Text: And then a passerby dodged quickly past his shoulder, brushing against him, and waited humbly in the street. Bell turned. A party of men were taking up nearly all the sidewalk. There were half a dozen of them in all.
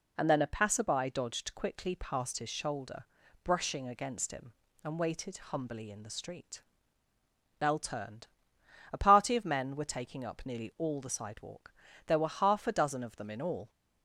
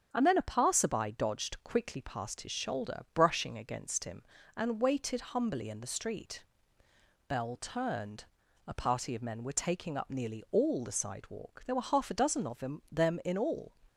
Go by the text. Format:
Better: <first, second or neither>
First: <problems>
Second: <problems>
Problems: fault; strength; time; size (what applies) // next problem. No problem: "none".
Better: first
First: none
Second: starts louder than the rest; strong; until 1.1 s; 8 dB // says "them" twice; at 12.9 s